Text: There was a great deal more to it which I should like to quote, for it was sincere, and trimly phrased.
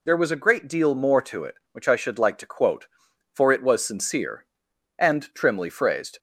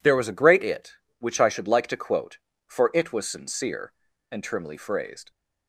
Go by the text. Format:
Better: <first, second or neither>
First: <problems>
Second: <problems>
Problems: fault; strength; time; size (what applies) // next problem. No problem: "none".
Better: first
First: none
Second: skips "deal more to"; at 0.6 s